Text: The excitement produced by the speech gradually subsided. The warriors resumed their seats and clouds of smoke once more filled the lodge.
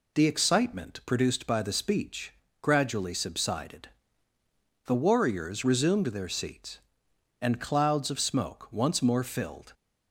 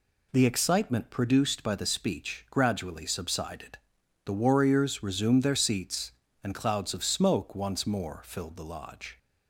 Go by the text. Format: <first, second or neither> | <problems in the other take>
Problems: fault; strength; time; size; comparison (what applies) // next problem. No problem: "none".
second | pauses between "speech" and "gradually"; slight; at 2.3 s; 0.30 s long // stops before "the lodge"; at 9.7 s